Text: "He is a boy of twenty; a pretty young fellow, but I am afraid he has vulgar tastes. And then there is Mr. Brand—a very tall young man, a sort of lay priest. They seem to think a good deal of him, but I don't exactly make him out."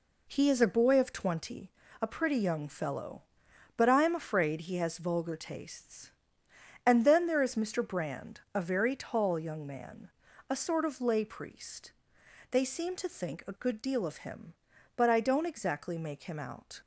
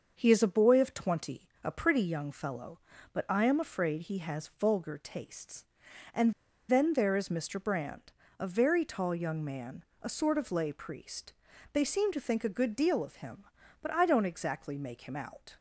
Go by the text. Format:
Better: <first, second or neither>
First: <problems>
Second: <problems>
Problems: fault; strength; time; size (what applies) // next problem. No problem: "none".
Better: first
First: none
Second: starts louder than the rest; until 1.1 s; 6.5 dB // pauses between "And" and "then"; at 6.3 s; 0.36 s long